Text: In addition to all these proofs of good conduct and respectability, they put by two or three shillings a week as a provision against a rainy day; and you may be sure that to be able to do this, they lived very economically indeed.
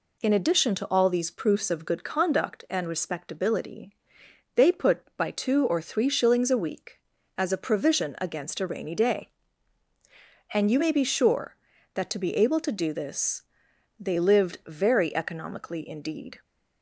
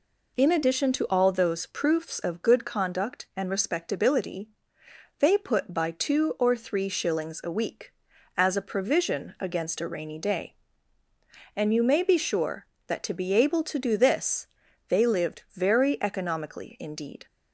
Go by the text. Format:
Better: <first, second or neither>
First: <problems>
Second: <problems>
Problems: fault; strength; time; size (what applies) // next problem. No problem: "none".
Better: first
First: none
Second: says "those" for "these"; at 1.2 s